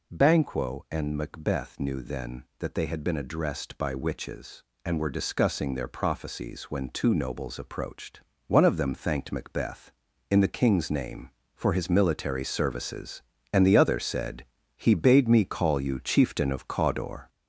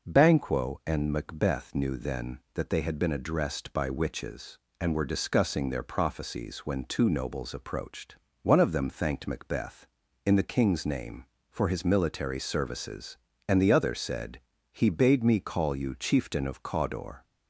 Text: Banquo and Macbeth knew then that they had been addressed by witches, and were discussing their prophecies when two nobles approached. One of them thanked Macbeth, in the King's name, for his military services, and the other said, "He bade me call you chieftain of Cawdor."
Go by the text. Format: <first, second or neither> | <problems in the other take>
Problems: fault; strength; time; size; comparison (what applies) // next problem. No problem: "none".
second | gets louder; noticeable; throughout; 5 dB